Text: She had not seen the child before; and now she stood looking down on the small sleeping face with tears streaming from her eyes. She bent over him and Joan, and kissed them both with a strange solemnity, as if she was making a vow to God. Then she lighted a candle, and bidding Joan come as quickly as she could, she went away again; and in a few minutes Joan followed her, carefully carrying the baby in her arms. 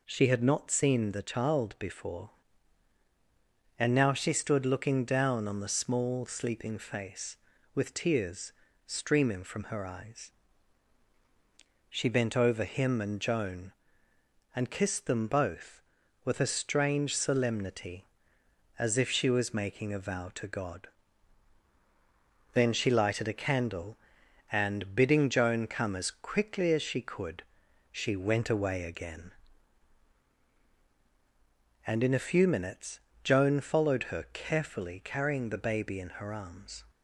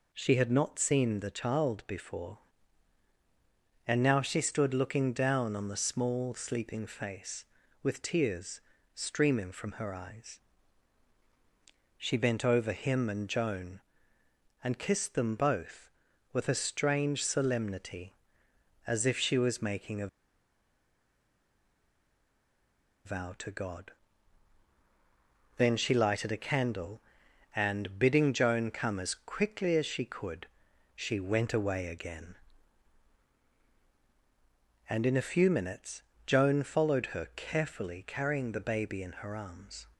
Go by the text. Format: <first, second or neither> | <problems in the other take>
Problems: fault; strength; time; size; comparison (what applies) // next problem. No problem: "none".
first | pauses between "tears" and "streaming"; slight; at 8.6 s; 0.32 s long; slight in the first // pauses between "a" and "vow"; strong; at 20.0 s; 2.9 s long // pauses between "minutes" and "Joan"; slight; at 36.0 s; 0.24 s long; slight in the first